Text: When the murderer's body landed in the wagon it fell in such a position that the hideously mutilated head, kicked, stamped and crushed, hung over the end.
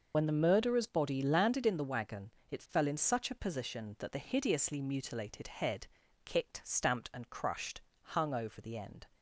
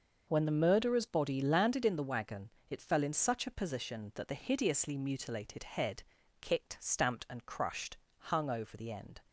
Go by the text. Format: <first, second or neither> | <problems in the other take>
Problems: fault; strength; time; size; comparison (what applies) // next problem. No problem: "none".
second | loses the start of "When"; at 0.1 s; 55 ms // pauses between "wagon" and "it"; slight; at 2.3 s; 0.18 s long; slight in the second